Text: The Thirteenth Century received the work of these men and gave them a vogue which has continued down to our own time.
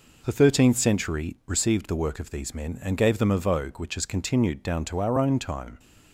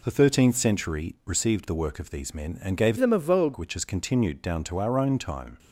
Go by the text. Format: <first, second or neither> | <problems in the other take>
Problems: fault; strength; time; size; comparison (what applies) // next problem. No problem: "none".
first | changes voice from "them" to "vogue"; from 2.9 to 3.5 s; 0.6 s long